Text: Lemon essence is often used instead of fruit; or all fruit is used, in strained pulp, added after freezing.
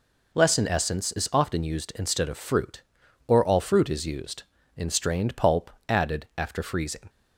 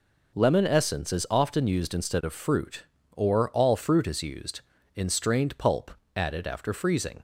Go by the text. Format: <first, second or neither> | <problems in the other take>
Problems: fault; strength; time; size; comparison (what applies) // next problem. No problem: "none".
second | says "Lesson" for "Lemon"; at 0.3 s